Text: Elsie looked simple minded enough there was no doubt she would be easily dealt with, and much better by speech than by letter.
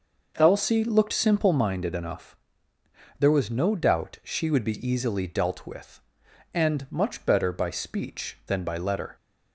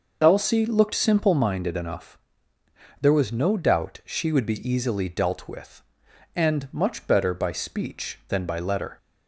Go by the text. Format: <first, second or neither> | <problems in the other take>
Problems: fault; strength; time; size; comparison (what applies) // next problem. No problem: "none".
first | loses the start of "Elsie"; at 0.2 s; 45 ms // pauses between "enough" and "there"; noticeable; at 2.1 s; 0.82 s long; noticeable in the first